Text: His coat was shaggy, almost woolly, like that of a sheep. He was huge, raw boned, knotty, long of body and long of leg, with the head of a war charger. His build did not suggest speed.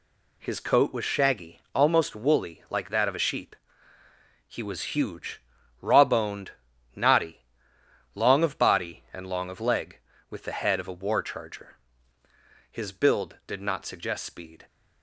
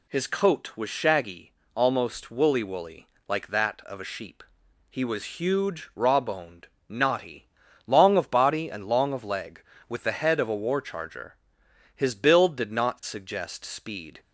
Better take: first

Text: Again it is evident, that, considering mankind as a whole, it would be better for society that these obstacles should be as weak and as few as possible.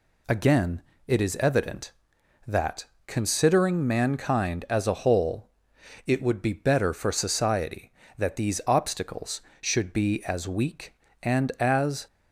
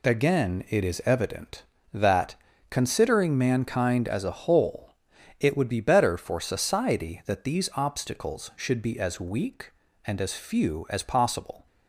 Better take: second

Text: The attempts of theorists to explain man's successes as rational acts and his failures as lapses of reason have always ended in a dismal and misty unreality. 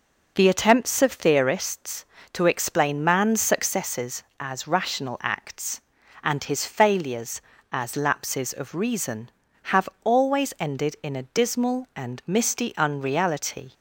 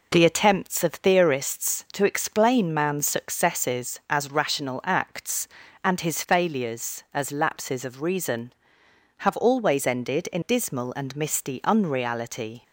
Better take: first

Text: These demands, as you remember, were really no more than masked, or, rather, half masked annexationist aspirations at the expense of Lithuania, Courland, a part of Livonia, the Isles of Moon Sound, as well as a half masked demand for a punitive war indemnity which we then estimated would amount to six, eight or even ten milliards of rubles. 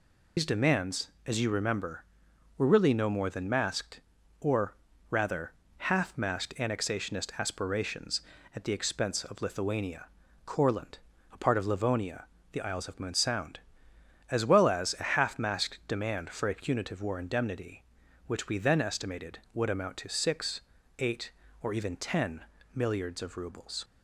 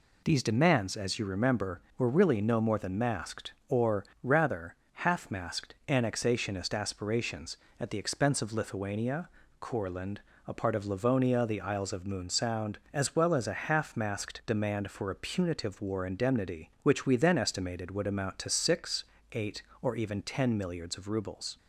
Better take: second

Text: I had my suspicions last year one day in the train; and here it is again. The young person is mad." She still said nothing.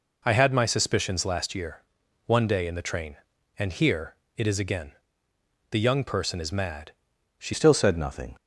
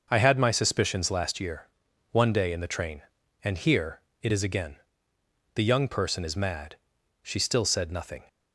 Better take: second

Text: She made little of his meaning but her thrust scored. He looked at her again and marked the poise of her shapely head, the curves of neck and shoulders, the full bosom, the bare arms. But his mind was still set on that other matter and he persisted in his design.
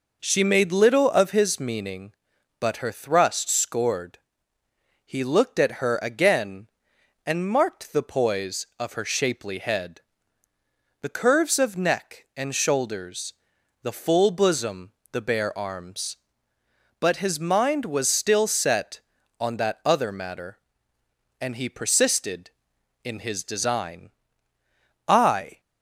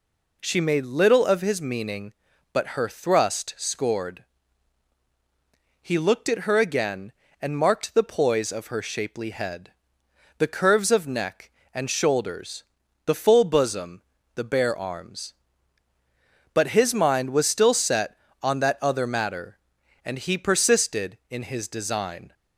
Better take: second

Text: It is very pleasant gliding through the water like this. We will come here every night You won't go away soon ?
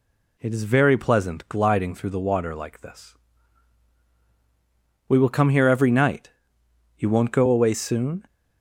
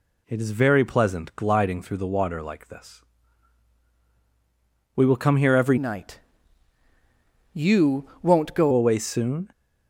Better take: first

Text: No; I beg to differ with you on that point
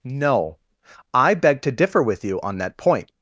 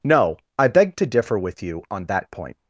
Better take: neither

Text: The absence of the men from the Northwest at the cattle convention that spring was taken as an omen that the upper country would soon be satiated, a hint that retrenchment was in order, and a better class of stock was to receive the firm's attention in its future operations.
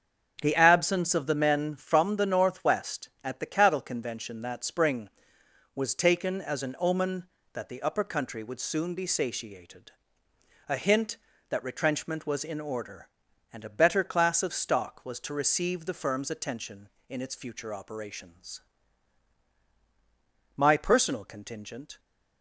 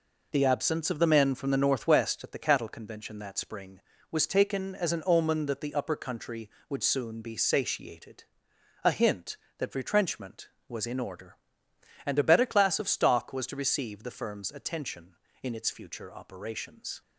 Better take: second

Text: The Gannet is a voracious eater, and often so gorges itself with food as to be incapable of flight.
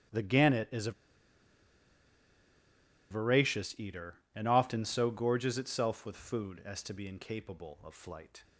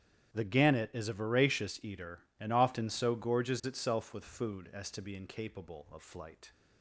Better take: second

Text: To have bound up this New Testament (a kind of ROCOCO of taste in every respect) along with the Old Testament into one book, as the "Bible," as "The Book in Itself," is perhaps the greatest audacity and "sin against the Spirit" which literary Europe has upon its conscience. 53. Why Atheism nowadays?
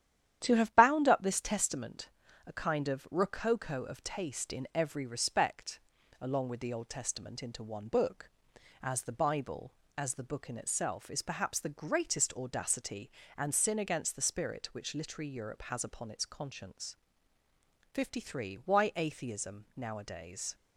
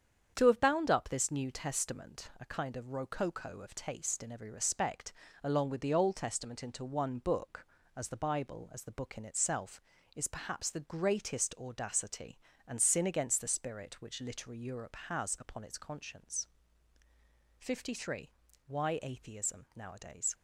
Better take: second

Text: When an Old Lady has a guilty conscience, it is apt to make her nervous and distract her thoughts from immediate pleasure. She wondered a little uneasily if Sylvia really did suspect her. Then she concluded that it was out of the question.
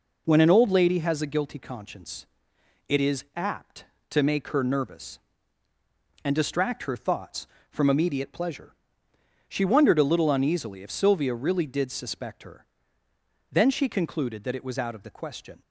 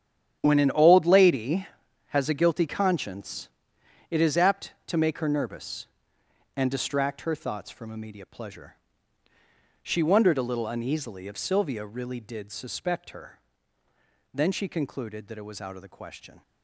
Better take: first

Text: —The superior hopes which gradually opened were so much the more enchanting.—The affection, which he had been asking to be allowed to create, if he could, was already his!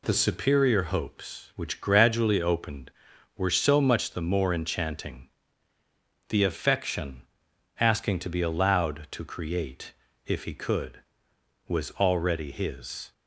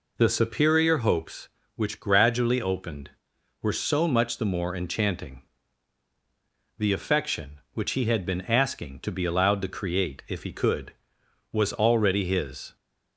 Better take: second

